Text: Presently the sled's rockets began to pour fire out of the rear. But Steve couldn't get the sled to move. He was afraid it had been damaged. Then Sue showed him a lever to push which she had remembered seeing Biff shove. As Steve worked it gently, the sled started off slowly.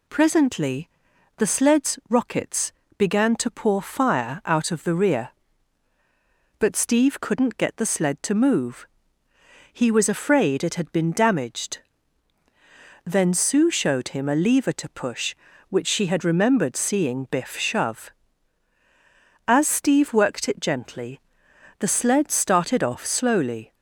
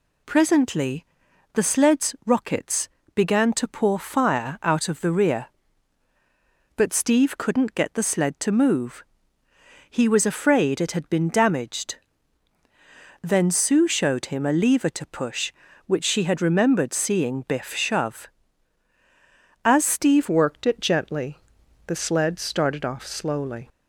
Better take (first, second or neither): first